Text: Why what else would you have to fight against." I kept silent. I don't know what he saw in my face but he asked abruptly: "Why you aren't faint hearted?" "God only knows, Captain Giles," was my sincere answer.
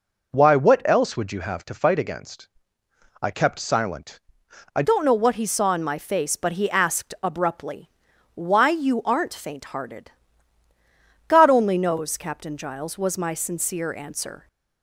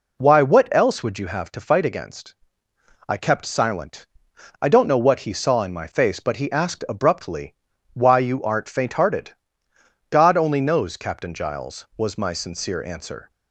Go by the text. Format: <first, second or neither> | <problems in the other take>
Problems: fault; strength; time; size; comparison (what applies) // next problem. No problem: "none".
second | changes voice at "don't"; from 4.8 s on; 9.6 s long